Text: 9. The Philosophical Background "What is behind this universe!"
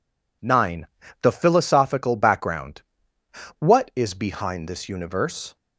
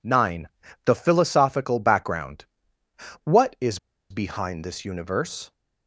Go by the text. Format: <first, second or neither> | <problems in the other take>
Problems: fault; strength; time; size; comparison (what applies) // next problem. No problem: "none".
first | pauses between "Background" and "What"; noticeable; at 2.4 s; 0.78 s long; noticeable in the first // pauses between "is" and "behind"; slight; at 3.7 s; 0.31 s long